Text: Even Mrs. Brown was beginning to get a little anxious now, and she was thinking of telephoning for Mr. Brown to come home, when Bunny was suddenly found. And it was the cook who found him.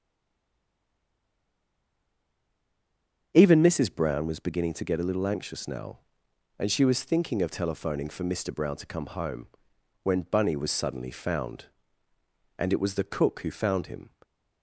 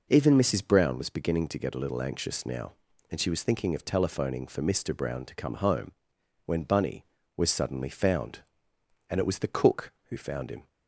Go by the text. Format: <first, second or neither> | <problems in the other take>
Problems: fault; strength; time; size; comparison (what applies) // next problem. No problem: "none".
second | stays silent before the first word; strong; until 3.3 s; 3.3 s long // starts louder than the rest; until 4.3 s; 7 dB